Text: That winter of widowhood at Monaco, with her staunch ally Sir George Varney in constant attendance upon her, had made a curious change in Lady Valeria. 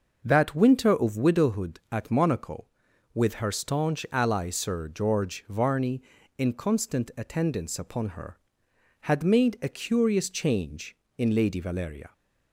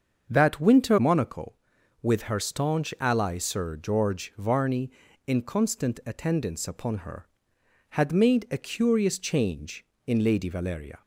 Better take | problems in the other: first | starts louder than the rest; until 1.3 s; 7 dB // skips "of widowhood at"; at 0.9 s

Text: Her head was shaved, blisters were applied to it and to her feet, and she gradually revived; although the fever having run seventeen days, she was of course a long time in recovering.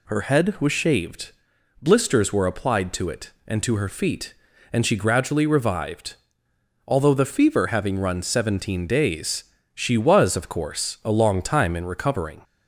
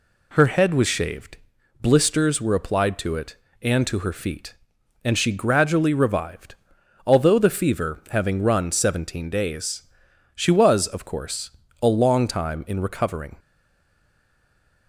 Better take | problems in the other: first | pauses between "course" and "a"; slight; at 11.4 s; 0.32 s long // stays silent after the last word; noticeable; from 13.3 s on; 1.5 s long

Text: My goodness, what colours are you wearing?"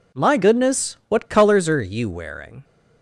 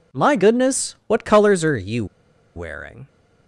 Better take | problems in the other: first | pauses between "you" and "wearing"; noticeable; at 2.0 s; 0.50 s long

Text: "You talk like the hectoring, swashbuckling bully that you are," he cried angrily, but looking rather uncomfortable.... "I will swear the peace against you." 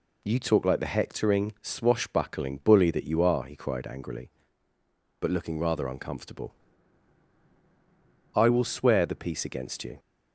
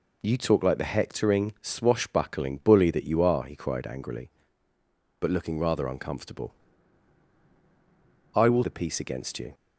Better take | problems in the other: first | skips "swear"; at 8.6 s

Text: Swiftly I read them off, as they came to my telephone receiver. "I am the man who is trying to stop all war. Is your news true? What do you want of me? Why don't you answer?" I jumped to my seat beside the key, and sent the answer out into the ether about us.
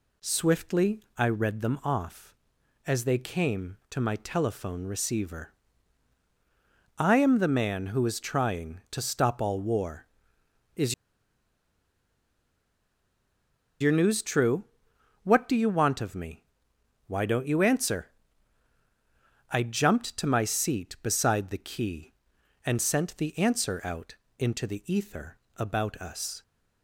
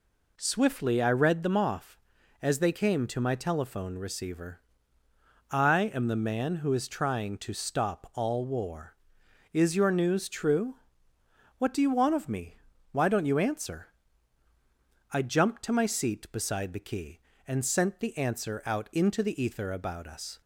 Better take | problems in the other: second | pauses between "Swiftly" and "I"; slight; at 0.9 s; 0.16 s long // pauses between "Is" and "your"; strong; at 10.9 s; 2.8 s long // pauses between "out" and "into"; slight; at 24.1 s; 0.24 s long // pauses between "ether" and "about"; slight; at 25.3 s; 0.18 s long

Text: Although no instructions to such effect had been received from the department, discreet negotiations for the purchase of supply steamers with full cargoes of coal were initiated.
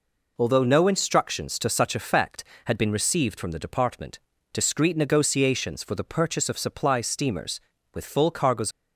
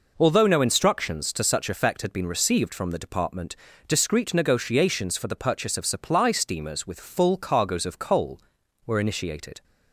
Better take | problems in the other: second | stops before "of coal were initiated"; at 8.7 s

